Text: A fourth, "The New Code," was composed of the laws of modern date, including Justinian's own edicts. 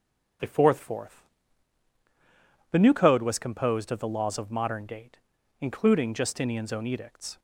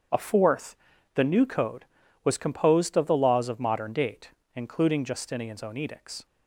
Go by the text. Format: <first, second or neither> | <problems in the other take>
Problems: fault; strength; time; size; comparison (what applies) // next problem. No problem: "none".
second | starts louder than the rest; until 2.9 s; 6.5 dB; strong in the second // says "fourth" twice; at 0.7 s